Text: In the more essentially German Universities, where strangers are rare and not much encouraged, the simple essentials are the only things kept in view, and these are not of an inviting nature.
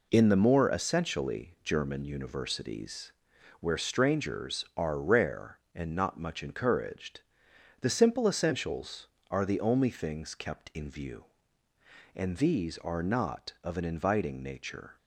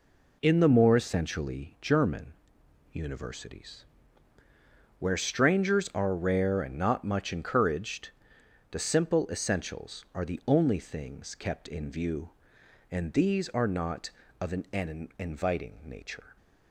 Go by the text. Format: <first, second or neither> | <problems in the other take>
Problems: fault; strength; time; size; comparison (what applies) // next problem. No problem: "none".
first | pauses between "German" and "Universities"; noticeable; at 2.3 s; 0.62 s long // says "an" twice; at 14.7 s